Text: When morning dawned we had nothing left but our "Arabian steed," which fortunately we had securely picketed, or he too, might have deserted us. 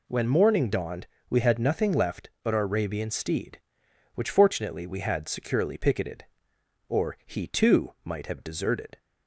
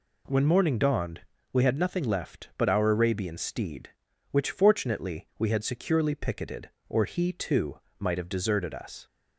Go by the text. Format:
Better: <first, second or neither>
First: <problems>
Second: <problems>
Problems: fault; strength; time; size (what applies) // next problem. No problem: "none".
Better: second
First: pauses between "dawned" and "we"; slight; at 1.0 s; 0.22 s long // stops before "us"; at 8.9 s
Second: pauses between "dawned" and "we"; slight; at 1.2 s; 0.32 s long